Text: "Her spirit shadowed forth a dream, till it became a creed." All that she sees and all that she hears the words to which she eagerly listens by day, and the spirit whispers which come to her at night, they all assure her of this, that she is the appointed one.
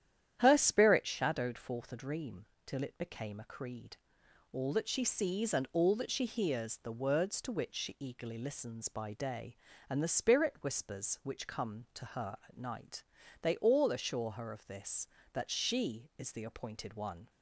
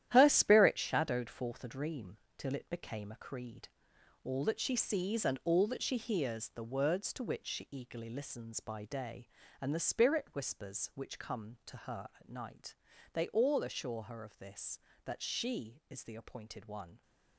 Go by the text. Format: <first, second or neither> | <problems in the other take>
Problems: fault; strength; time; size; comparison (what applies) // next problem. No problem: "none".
first | gets quieter; strong; throughout; 10 dB // starts louder than the rest; strong; until 1.1 s; 11.5 dB; strong in the first